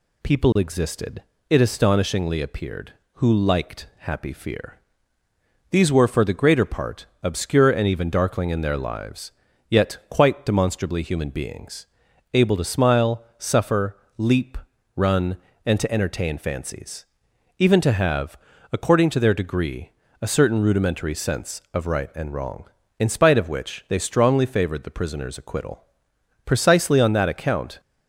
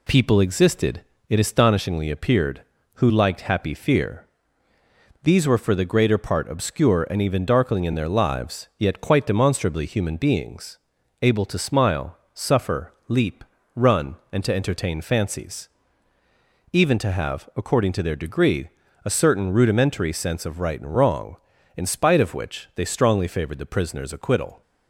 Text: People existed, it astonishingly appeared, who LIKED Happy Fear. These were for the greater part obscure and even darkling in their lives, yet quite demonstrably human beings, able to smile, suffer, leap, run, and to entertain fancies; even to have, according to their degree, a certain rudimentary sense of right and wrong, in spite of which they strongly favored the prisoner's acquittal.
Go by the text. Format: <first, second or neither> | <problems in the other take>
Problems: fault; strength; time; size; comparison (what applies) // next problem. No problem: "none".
second | pauses between "part" and "obscure"; slight; at 7.0 s; 0.16 s long // goes on to say "Precisely on that account"; from 26.4 s on; 1.3 s long